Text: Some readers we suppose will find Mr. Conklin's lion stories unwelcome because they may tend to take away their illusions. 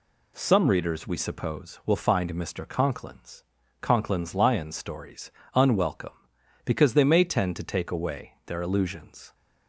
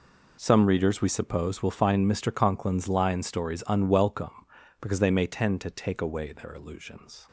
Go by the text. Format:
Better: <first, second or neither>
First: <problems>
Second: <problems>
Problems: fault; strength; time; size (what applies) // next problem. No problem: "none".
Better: second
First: says "Conklin's" twice; at 3.8 s // pauses between "stories" and "unwelcome"; slight; at 5.3 s; 0.24 s long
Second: none